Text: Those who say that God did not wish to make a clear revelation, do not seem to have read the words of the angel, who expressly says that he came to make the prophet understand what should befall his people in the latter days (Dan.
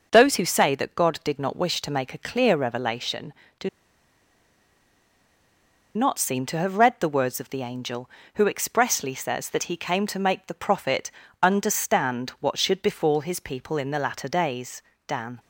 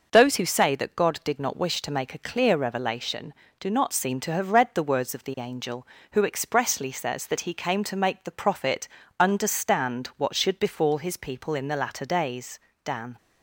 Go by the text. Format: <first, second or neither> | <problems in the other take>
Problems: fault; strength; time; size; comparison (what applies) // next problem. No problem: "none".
second | pauses between "do" and "not"; strong; at 3.6 s; 2.2 s long // pauses between "prophet" and "understand"; slight; at 11.0 s; 0.32 s long; slight in the second